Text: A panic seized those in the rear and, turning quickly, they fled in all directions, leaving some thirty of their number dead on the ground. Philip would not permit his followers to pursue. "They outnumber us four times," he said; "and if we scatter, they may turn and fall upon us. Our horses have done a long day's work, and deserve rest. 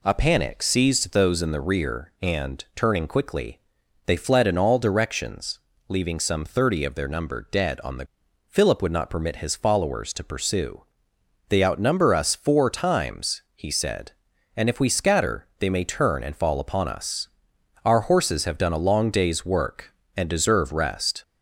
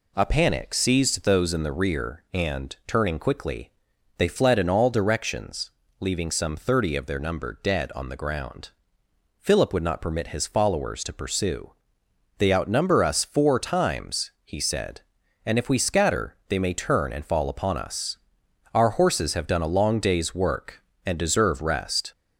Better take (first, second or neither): second